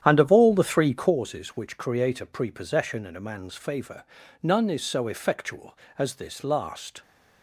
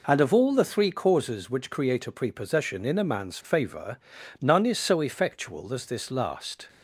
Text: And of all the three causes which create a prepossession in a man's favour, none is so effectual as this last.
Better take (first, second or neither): second